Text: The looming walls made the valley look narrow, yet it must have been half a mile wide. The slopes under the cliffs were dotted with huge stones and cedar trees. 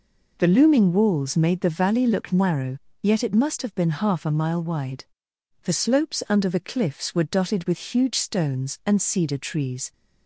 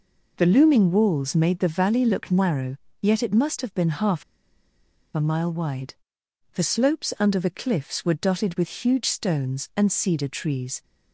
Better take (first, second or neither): first